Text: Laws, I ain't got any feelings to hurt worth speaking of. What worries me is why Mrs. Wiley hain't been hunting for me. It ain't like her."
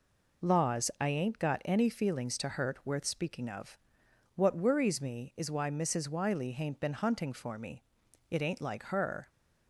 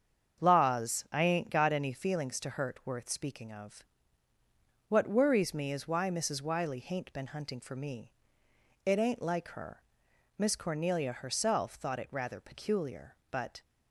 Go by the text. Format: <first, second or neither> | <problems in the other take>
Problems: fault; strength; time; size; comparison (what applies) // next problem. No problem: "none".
first | starts louder than the rest; strong; until 1.4 s; 7 dB // goes on to say "Miss Cornelia herself thought it rather peculiar but"; strong; from 10.3 s on; 3.2 s long